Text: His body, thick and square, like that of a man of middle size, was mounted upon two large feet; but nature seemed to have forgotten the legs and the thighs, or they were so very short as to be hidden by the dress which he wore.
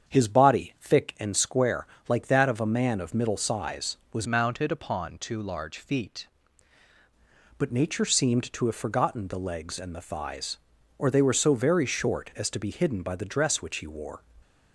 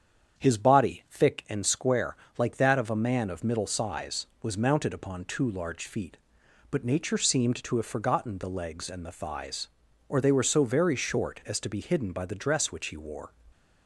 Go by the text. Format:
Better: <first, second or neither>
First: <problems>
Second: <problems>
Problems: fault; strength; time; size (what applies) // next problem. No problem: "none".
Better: second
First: starts louder than the rest; strong; until 1.2 s; 7.5 dB // changes voice from "mounted" to "feet"; from 4.2 to 6.2 s; 2.0 s long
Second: starts louder than the rest; strong; until 1.5 s; 8 dB